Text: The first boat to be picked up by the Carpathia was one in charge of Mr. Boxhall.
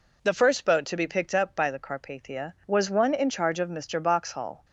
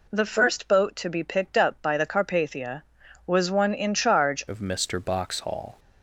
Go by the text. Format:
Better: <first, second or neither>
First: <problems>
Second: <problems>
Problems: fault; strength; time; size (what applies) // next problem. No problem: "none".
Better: first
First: none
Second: changes voice at "of"; from 4.4 s on; 1.3 s long